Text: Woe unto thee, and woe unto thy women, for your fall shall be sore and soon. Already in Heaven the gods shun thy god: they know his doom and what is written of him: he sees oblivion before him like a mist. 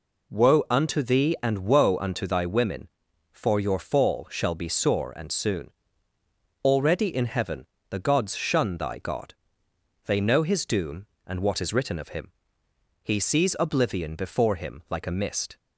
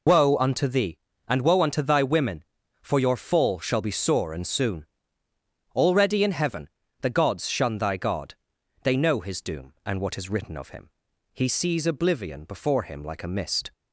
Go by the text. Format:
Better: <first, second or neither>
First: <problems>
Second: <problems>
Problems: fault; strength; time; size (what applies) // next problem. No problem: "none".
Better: first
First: pauses between "Heaven" and "the"; slight; at 7.6 s; 0.24 s long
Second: loses the start of "Woe"; at 0.0 s; 80 ms // pauses between "Heaven" and "the"; slight; at 6.6 s; 0.32 s long